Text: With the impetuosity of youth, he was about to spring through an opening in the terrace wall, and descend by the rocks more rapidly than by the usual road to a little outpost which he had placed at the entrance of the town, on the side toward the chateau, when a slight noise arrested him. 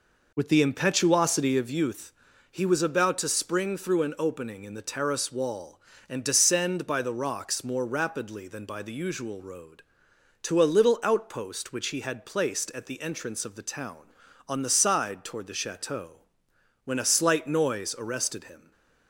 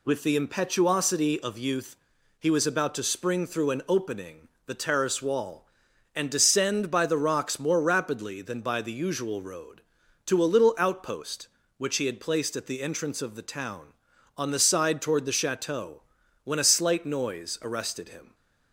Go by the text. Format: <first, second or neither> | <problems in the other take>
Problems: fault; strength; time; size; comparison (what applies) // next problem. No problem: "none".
first | skips "in"; at 4.5 s